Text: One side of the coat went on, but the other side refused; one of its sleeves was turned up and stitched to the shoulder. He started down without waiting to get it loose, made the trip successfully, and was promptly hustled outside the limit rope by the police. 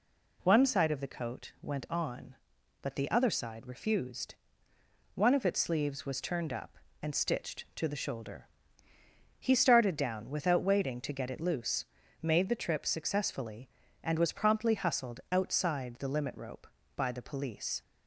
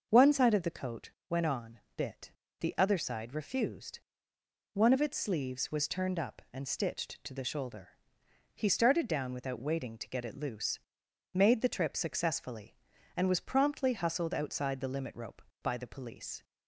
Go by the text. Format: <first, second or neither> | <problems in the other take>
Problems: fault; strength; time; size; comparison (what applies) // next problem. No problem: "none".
first | starts louder than the rest; until 1.1 s; 6.5 dB // pauses between "coat" and "went"; slight; at 1.1 s; 0.20 s long // says "bit" for "but"; at 1.9 s